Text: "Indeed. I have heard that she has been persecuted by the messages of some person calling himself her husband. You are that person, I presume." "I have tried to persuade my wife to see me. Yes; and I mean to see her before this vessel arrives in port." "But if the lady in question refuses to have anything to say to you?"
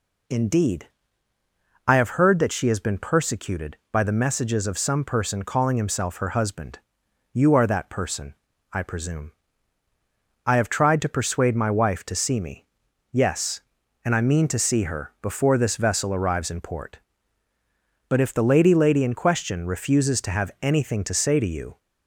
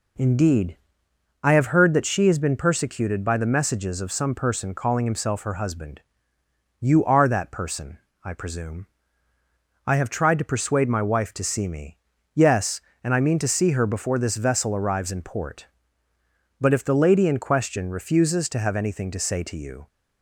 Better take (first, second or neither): second